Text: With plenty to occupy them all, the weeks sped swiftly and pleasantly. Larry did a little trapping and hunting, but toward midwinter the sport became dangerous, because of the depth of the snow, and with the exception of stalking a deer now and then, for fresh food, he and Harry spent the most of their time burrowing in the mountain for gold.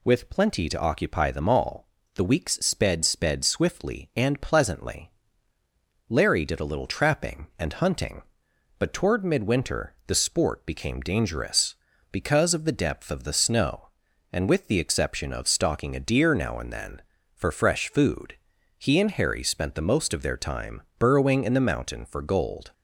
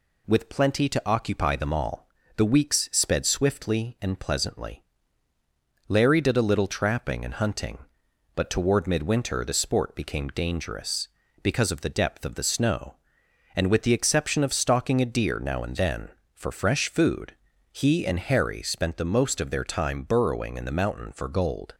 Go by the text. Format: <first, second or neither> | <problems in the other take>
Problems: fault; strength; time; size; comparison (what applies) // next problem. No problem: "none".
second | says "sped" twice; at 3.0 s // pauses between "time" and "burrowing"; slight; at 20.8 s; 0.18 s long